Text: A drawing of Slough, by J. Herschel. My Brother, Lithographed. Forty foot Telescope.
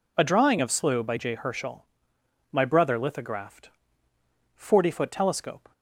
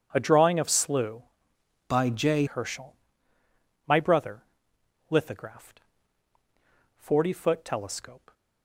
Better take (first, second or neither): first